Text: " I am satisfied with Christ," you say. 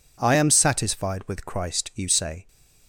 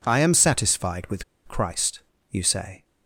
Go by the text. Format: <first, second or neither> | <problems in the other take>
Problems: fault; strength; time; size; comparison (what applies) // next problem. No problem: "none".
first | pauses between "with" and "Christ"; slight; at 1.2 s; 0.24 s long